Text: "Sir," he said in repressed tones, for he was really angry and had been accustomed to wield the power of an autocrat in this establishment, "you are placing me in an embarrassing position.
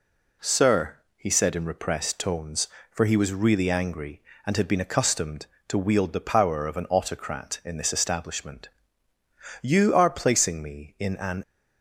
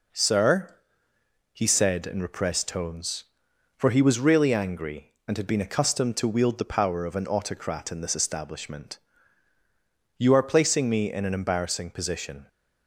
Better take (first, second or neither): second